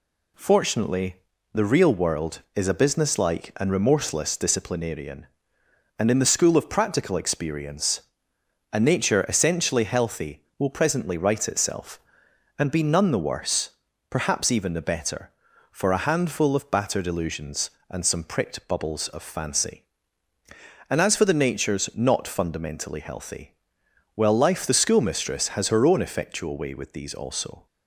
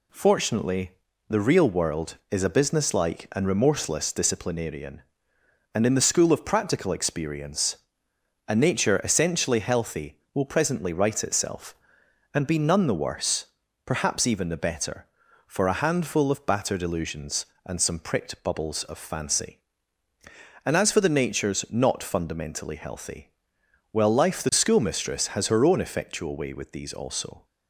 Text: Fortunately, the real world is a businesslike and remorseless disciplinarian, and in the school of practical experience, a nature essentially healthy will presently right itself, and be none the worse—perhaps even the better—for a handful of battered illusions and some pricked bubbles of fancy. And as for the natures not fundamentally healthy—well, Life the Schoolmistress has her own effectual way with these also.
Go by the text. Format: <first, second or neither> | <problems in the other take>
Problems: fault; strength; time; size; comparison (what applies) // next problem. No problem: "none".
neither | none